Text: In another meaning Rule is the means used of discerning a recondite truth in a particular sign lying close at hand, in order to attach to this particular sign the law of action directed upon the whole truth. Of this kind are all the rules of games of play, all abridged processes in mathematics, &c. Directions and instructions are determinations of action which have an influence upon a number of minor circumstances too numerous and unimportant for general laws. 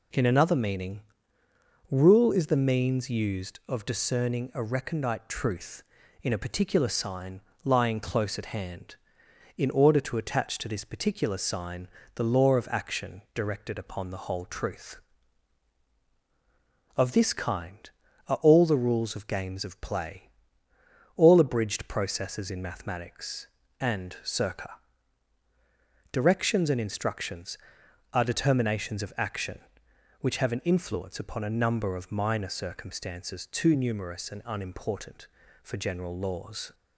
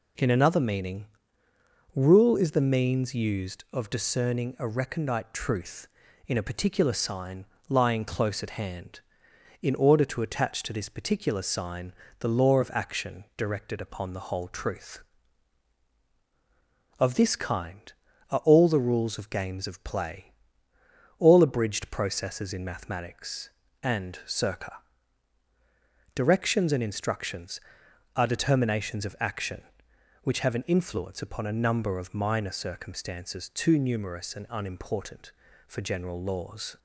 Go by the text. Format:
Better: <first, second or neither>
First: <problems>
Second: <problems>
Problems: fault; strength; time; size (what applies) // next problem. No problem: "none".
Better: neither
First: pauses between "meaning" and "Rule"; noticeable; at 1.0 s; 0.88 s long // pauses between "sign" and "lying"; slight; at 7.3 s; 0.24 s long // pauses between "sign" and "the"; slight; at 11.8 s; 0.28 s long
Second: pauses between "meaning" and "Rule"; noticeable; at 1.0 s; 0.88 s long // pauses between "sign" and "lying"; slight; at 7.4 s; 0.24 s long // pauses between "sign" and "the"; slight; at 11.9 s; 0.28 s long